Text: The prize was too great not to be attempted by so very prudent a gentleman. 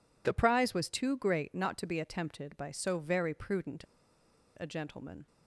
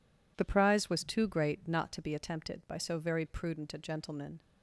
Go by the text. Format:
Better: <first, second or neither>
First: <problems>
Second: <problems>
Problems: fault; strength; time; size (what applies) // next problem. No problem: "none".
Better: second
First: pauses between "prudent" and "a"; noticeable; at 3.8 s; 0.74 s long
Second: none